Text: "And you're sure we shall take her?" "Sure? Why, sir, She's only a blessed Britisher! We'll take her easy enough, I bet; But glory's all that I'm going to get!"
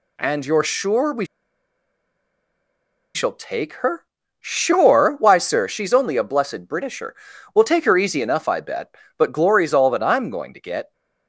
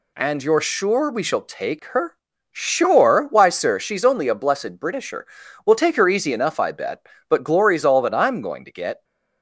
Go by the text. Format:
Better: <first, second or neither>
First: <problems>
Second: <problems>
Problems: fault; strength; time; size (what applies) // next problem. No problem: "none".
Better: second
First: pauses between "we" and "shall"; strong; at 1.2 s; 1.8 s long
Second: none